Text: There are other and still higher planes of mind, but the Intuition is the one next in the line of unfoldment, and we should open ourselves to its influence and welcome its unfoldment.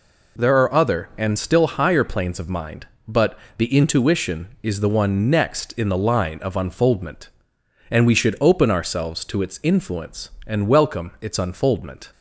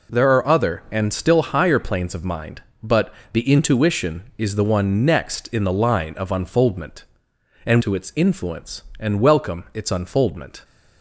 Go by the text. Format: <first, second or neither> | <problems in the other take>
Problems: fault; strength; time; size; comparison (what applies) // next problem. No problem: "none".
first | pauses between "but" and "the"; slight; at 3.1 s; 0.16 s long; slight in the first // skips "we should open ourselves"; at 7.8 s